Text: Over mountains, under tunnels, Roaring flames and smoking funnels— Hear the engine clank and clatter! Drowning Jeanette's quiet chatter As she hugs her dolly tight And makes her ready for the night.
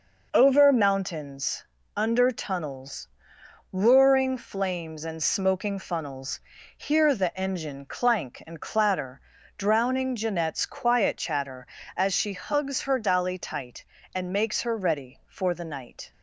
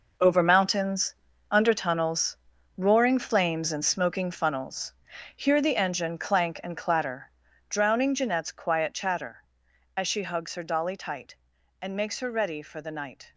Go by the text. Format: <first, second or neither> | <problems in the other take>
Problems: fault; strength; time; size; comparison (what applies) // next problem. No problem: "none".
first | gets quieter; strong; throughout; 11.5 dB